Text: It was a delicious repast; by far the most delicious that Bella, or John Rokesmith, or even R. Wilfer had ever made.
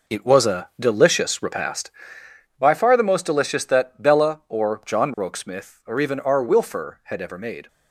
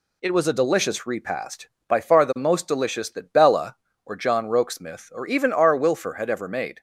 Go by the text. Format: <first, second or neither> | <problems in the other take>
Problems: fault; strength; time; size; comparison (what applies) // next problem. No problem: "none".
second | gets quieter; strong; throughout; 8.5 dB